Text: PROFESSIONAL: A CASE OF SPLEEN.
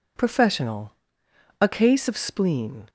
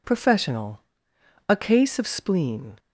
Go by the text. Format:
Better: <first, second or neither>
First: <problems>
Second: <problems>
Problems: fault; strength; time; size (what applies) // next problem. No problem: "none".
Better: neither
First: none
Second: none